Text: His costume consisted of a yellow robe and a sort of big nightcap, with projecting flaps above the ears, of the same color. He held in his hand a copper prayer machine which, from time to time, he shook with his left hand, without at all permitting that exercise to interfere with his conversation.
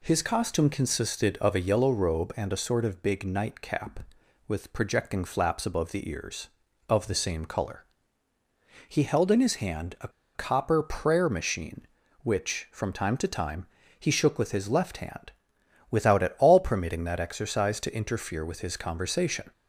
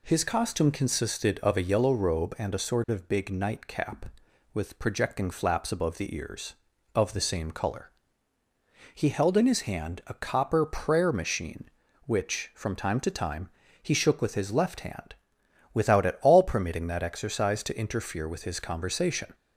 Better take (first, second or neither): second